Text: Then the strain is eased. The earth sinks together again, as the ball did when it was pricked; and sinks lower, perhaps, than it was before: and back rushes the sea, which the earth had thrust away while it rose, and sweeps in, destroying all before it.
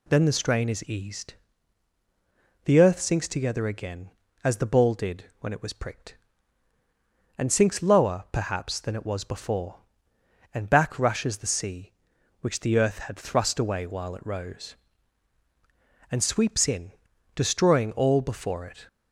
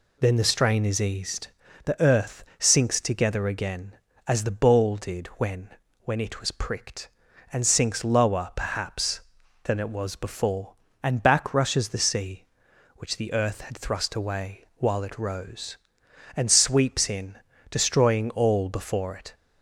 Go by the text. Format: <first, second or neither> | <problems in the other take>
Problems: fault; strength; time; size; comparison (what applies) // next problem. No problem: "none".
first | says "when" twice; at 6.0 s